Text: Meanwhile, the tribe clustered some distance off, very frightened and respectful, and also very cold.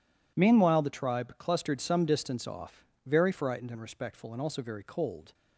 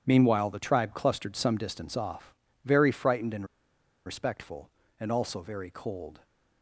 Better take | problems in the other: first | pauses between "and" and "respectful"; noticeable; at 3.4 s; 0.61 s long

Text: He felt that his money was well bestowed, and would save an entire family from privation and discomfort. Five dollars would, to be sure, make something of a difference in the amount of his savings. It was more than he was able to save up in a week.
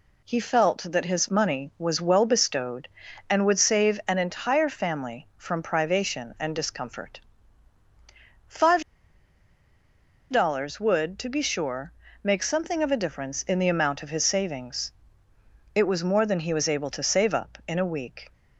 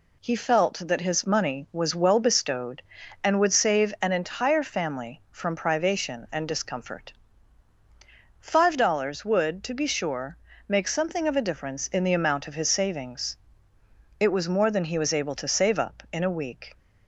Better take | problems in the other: second | pauses between "Five" and "dollars"; strong; at 8.8 s; 1.4 s long

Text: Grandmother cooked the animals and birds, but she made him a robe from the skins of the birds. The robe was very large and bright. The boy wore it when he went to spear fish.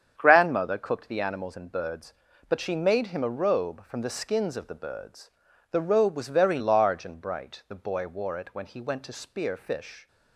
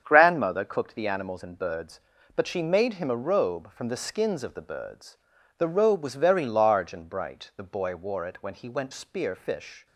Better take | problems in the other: first | starts louder than the rest; strong; until 1.0 s; 8 dB; strong in the first // skips "to"; at 8.9 s

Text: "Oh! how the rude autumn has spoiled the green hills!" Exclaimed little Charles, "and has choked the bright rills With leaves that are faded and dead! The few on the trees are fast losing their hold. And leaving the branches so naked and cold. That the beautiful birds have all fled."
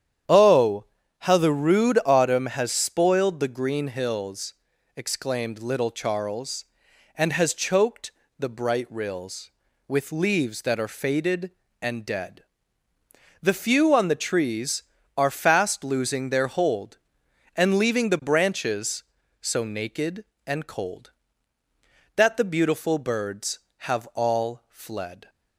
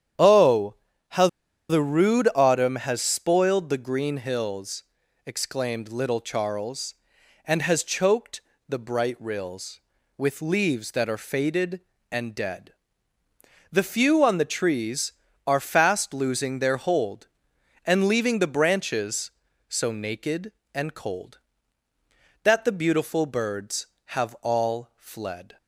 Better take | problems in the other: first | starts louder than the rest; strong; until 1.9 s; 9.5 dB; strong in the first // pauses between "how" and "the"; at 1.2 s; 0.42 s long // pauses between "choked" and "the"; slight; at 8.3 s; 0.30 s long; slight in the first

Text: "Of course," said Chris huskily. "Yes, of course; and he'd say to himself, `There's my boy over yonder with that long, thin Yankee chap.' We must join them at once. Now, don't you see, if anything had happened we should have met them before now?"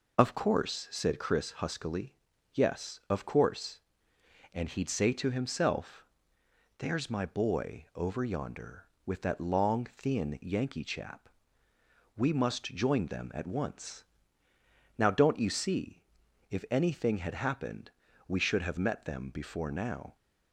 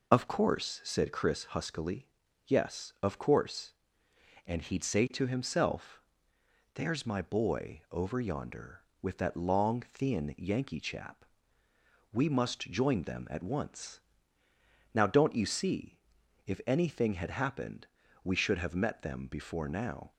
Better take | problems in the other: neither | pauses between "happened" and "we"; slight; the same in both

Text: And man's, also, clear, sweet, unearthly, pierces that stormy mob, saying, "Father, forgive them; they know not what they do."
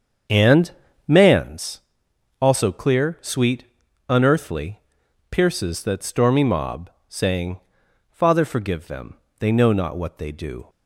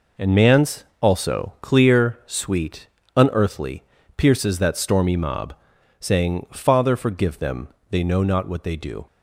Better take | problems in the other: second | starts louder than the rest; strong; until 1.6 s; 7 dB // pauses between "And" and "man's"; slight; at 0.7 s; 0.36 s long

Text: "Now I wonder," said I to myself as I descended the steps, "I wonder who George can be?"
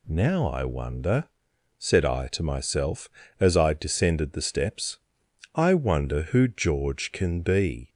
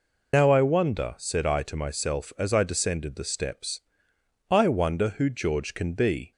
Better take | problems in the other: first | loses the start of "Now"; at 0.3 s; 80 ms

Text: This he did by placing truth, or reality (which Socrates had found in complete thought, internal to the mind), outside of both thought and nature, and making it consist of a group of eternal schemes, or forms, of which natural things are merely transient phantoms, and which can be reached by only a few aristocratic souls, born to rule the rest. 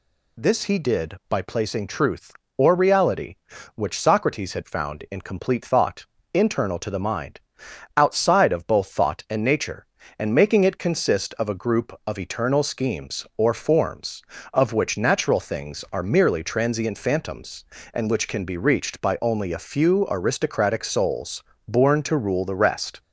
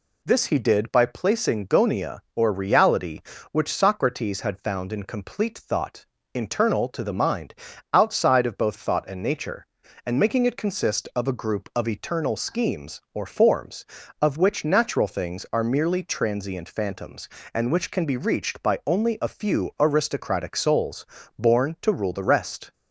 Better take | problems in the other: first | says "gonia" for "truth"; at 1.6 s

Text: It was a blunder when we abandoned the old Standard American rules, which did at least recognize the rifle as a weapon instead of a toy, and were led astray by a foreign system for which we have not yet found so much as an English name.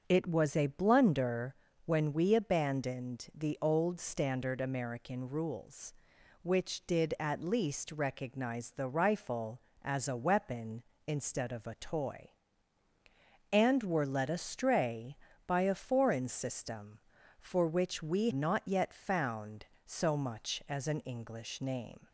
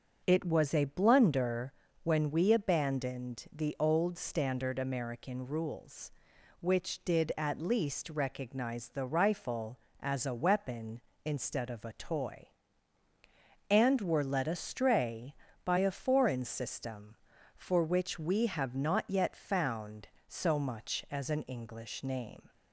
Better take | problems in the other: second | starts louder than the rest; until 1.0 s; 7 dB; also in the second // pauses between "blunder" and "when"; slight; at 1.5 s; 0.32 s long; slight in the second // skips "have"; at 18.3 s

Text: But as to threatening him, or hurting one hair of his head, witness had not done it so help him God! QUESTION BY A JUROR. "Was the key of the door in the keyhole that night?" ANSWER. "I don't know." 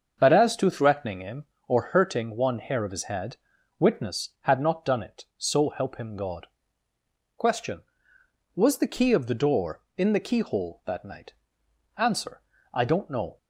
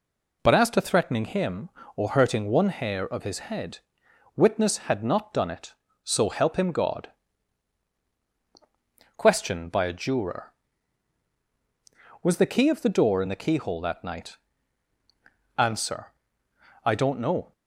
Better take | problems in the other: second | starts louder than the rest; until 1.2 s; 7 dB // skips "BY A JUROR"; at 8.1 s

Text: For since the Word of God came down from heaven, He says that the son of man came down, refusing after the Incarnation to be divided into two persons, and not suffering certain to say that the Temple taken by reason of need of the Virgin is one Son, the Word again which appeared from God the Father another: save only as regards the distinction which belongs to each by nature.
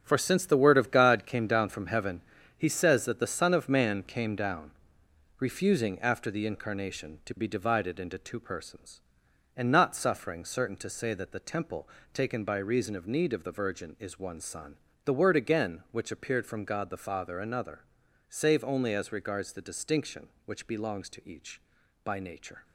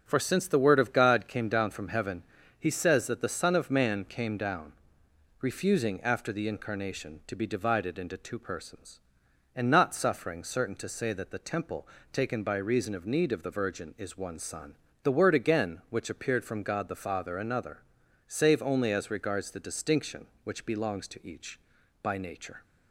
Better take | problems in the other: second | gets quieter; strong; throughout; 8.5 dB // starts louder than the rest; strong; until 1.0 s; 8.5 dB; strong in the second // pauses between "Temple" and "taken"; slight; at 11.8 s; 0.24 s long; slight in the second

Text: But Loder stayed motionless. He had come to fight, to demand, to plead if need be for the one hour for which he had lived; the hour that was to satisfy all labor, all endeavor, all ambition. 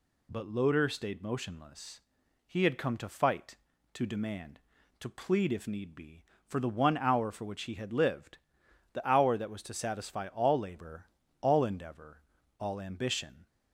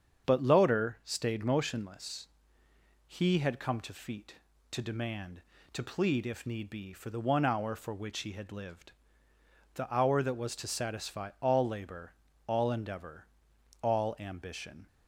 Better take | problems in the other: first | starts louder than the rest; strong; until 1.3 s; 7.5 dB // says "feet" for "fight"; at 3.9 s

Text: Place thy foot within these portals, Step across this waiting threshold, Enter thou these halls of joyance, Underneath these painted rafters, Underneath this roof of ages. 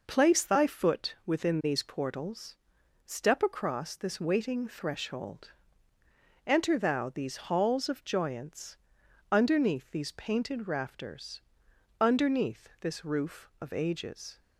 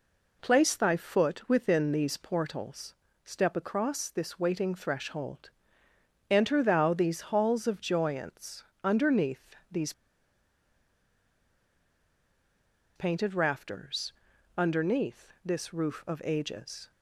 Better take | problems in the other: first | pauses between "Underneath" and "these"; slight; at 9.5 s; 0.16 s long // pauses between "these" and "painted"; strong; at 9.9 s; 3.0 s long

